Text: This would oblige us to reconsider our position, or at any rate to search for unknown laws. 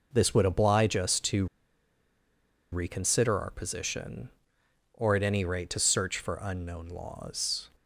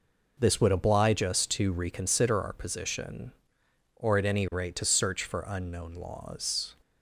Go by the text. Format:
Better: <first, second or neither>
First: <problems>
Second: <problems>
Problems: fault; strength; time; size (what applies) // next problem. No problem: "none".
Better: second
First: pauses between "to" and "reconsider"; strong; at 1.4 s; 1.2 s long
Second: none